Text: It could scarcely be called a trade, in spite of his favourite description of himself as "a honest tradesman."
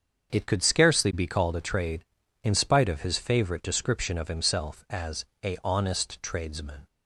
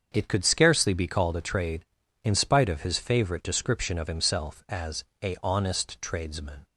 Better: neither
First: starts louder than the rest; until 1.3 s; 7 dB // pauses between "as" and "a"; slight; at 5.2 s; 0.18 s long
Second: starts louder than the rest; until 1.1 s; 7 dB // pauses between "as" and "a"; slight; at 5.0 s; 0.18 s long

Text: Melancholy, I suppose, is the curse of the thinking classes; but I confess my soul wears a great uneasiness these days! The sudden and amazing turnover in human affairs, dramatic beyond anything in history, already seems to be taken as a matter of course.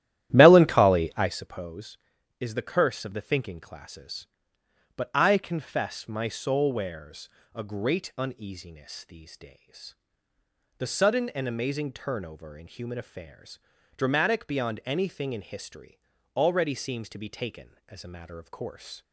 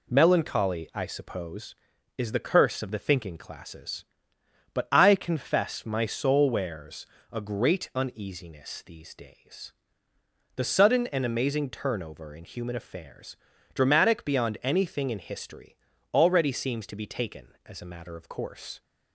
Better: second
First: starts louder than the rest; strong; until 1.5 s; 12.5 dB // pauses between "wears" and "a"; slight; at 7.2 s; 0.26 s long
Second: pauses between "wears" and "a"; slight; at 7.0 s; 0.26 s long

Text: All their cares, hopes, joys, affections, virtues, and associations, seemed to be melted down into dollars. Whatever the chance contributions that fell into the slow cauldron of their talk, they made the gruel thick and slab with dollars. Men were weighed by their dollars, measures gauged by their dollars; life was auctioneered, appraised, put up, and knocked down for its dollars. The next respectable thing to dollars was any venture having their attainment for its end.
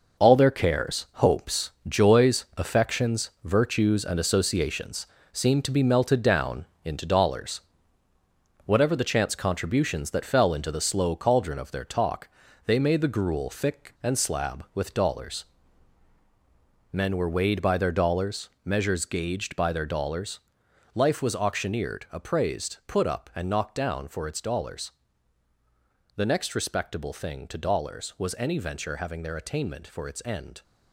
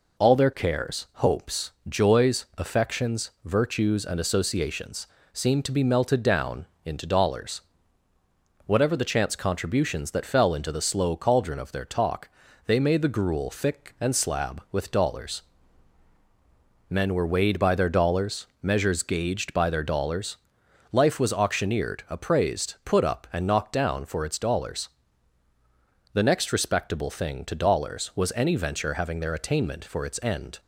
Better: second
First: gets quieter; strong; throughout; 8 dB // pauses between "down" and "into"; slight; at 6.6 s; 0.18 s long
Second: pauses between "down" and "into"; slight; at 6.6 s; 0.18 s long

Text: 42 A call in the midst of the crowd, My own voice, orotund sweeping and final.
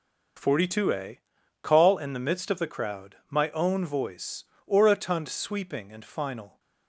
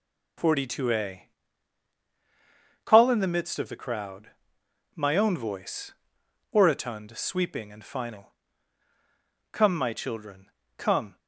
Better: first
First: pauses between "A" and "call"; at 1.1 s; 0.44 s long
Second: pauses between "A" and "call"; strong; at 1.2 s; 1.5 s long // goes on to say "Come my children Come"; strong; from 9.5 s on; 1.6 s long

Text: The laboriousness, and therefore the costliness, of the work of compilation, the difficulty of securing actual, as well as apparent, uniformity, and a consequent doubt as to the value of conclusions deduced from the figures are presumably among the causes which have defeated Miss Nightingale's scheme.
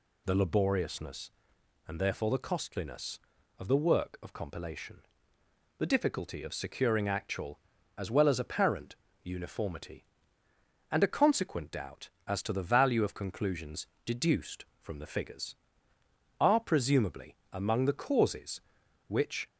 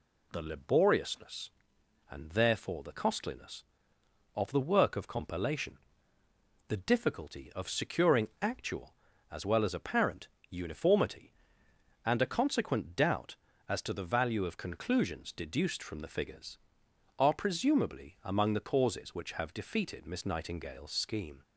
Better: second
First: pauses between "conclusions" and "deduced"; slight; at 13.8 s; 0.20 s long // pauses between "presumably" and "among"; slight; at 17.3 s; 0.16 s long // stops before "have defeated Miss Nightingale's scheme"; at 19.4 s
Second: none

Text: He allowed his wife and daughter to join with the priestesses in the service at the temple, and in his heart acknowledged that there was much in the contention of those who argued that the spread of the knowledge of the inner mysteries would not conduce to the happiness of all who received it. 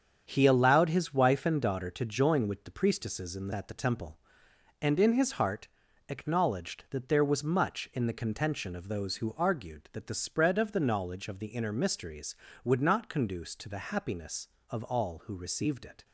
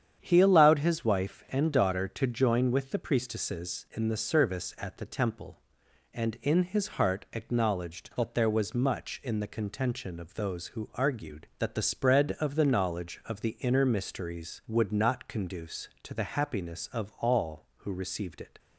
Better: second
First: starts louder than the rest; strong; until 1.2 s; 7.5 dB // skips "service"; at 3.5 s // pauses between "heart" and "acknowledged"; at 5.6 s; 0.42 s long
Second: starts louder than the rest; strong; until 1.2 s; 8.5 dB

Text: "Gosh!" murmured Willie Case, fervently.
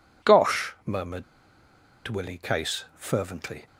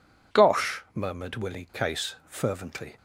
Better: second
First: pauses between "murmured" and "Willie"; noticeable; at 1.2 s; 0.84 s long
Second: none

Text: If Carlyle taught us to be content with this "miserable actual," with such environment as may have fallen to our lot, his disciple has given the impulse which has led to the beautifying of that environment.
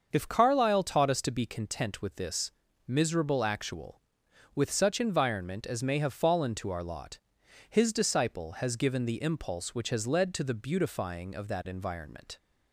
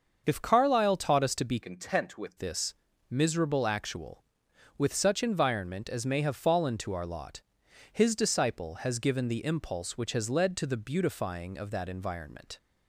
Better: first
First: starts louder than the rest; until 1.1 s; 6.5 dB // pauses between "this" and "miserable"; slight; at 2.5 s; 0.34 s long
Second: starts louder than the rest; until 1.2 s; 6.5 dB // changes voice from "content" to "with"; from 1.6 to 2.3 s; 0.7 s long // pauses between "this" and "miserable"; slight; at 2.7 s; 0.34 s long

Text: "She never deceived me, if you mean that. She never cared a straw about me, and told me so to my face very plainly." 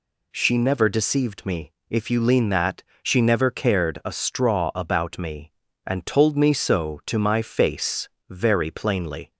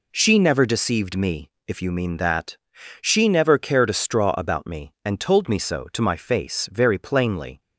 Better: second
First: says "lean" for "mean"; at 2.2 s // pauses between "face" and "very"; slight; at 8.0 s; 0.22 s long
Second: none

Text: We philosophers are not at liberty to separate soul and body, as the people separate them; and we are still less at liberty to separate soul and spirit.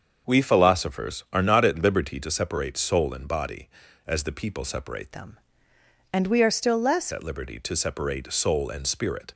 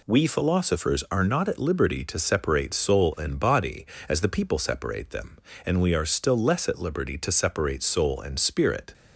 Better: second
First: starts louder than the rest; until 1.3 s; 6.5 dB // changes voice from "them" to "less"; from 5.1 to 7.1 s; 2.0 s long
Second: none

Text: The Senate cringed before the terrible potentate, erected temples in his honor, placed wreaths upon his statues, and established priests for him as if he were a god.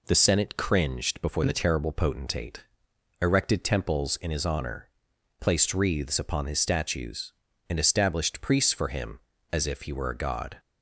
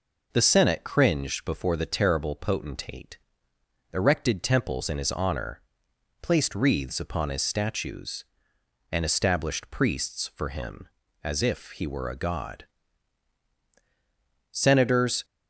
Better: first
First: none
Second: goes on to say "Senators"; noticeable; from 14.5 s on; 0.74 s long

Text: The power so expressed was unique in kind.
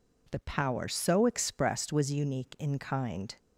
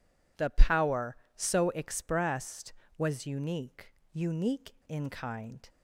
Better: first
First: none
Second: says "unique" twice; at 4.1 s

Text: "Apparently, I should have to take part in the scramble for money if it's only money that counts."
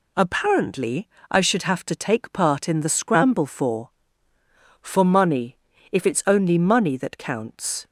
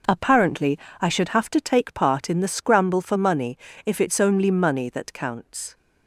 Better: second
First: says "for" twice; at 4.8 s // pauses between "money" and "if"; slight; at 5.5 s; 0.36 s long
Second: pauses between "money" and "if"; slight; at 3.5 s; 0.28 s long

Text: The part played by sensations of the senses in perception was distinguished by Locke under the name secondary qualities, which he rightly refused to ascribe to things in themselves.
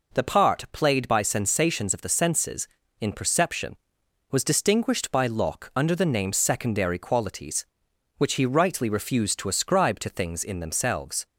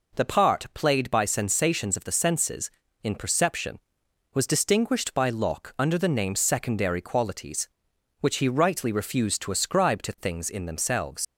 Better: first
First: none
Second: leaves "themselves" unfinished; at 11.2 s; 60 ms

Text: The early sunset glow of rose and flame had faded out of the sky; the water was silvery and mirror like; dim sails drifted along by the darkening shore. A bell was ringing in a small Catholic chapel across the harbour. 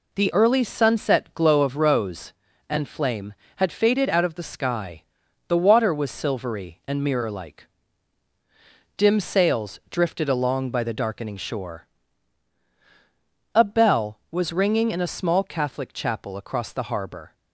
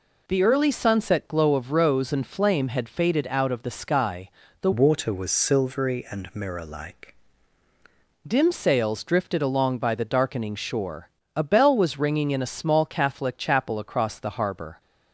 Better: first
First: none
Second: changes voice from "water" to "like"; from 4.7 to 7.1 s; 2.4 s long

